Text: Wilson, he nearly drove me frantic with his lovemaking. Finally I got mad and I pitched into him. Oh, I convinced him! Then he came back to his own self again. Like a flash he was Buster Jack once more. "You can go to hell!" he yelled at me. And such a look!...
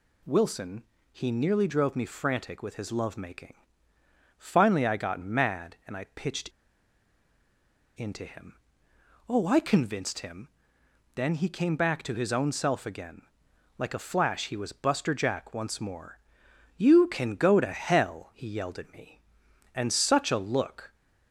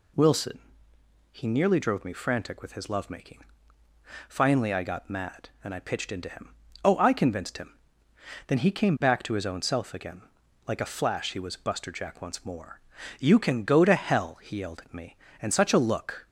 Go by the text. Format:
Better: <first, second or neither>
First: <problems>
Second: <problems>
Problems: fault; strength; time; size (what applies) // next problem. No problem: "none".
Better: second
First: pauses between "pitched" and "into"; strong; at 6.4 s; 1.4 s long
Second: none